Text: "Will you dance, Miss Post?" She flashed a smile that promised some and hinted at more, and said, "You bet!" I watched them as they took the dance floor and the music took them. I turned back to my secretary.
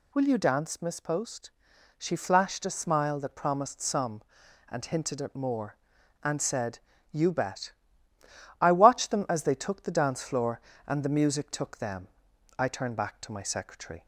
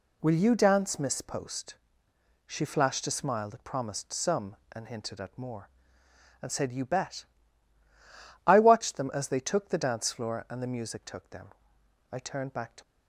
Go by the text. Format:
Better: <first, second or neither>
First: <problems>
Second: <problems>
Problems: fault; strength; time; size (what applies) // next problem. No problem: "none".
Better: first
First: none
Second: stops before "my secretary"; at 12.8 s